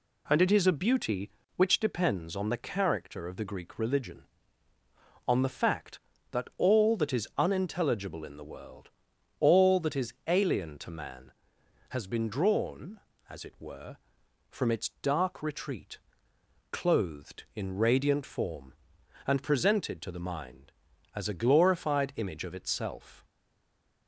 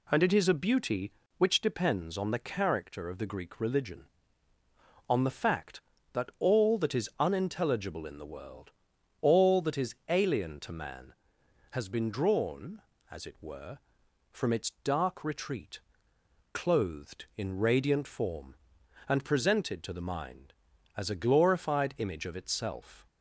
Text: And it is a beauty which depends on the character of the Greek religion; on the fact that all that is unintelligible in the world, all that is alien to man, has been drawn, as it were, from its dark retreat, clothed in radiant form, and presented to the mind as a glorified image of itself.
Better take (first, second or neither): second